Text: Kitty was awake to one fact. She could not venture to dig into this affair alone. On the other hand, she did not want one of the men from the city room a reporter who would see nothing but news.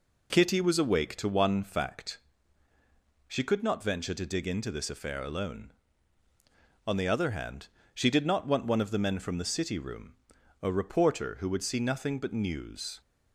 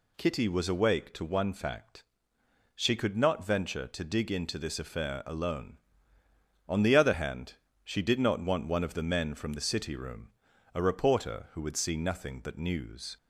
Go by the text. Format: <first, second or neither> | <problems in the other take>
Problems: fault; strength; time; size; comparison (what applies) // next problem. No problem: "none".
neither | pauses between "room" and "a"; the same in both